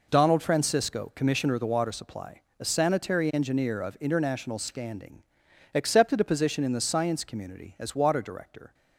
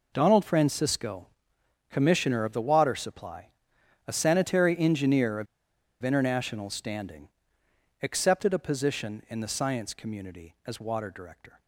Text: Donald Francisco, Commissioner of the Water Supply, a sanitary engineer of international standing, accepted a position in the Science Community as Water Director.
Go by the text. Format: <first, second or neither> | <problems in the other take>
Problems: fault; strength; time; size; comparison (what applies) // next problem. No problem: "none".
first | pauses between "of" and "international"; noticeable; at 5.4 s; 0.56 s long